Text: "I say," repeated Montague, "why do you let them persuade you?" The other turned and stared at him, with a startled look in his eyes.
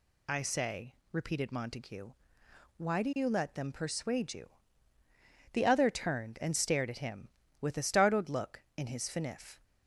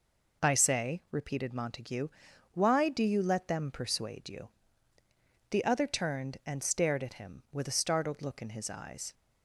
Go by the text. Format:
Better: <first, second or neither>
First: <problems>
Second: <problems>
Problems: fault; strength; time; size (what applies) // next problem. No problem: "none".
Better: second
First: says "finif" for "eyes"; at 9.0 s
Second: none